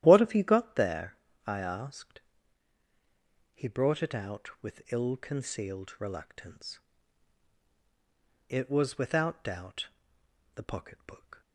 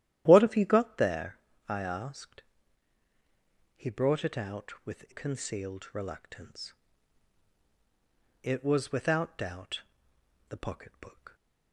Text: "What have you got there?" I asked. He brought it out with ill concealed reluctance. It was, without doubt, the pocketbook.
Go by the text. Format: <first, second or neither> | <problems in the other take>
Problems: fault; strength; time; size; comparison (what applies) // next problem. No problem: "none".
first | starts louder than the rest; strong; until 1.2 s; 12.5 dB; strong in the first // skips "ill"; at 5.1 s